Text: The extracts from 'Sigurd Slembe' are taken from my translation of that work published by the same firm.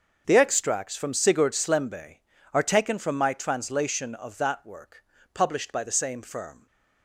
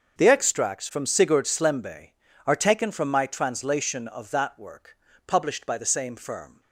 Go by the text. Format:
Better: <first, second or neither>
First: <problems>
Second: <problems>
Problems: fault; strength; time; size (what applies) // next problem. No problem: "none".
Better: neither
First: starts louder than the rest; until 1.2 s; 6.5 dB // pauses between "work" and "published"; slight; at 5.0 s; 0.30 s long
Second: starts louder than the rest; until 1.2 s; 6.5 dB // pauses between "work" and "published"; slight; at 4.9 s; 0.30 s long